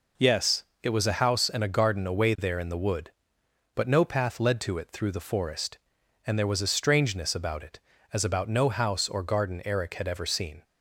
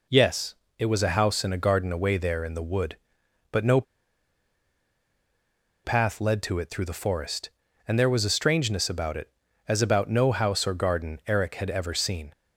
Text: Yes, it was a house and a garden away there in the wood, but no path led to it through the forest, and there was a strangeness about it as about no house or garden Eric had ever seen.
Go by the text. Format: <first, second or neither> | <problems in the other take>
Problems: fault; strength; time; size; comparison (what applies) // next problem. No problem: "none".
first | pauses between "no" and "path"; strong; at 3.8 s; 2.0 s long